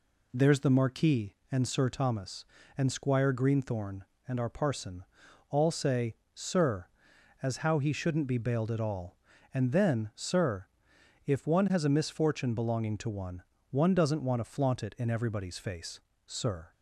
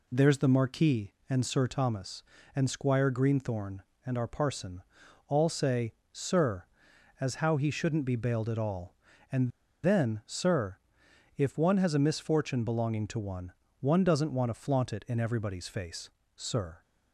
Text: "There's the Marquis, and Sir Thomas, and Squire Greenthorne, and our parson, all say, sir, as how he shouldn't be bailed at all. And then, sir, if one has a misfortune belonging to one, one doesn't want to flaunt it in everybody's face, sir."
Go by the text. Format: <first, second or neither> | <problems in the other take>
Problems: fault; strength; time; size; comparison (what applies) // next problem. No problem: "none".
first | pauses between "And" and "then"; slight; at 9.4 s; 0.33 s long